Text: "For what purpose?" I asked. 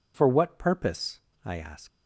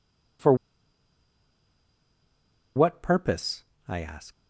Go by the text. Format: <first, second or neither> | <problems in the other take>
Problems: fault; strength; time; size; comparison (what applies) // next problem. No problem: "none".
first | pauses between "For" and "what"; strong; at 0.5 s; 2.2 s long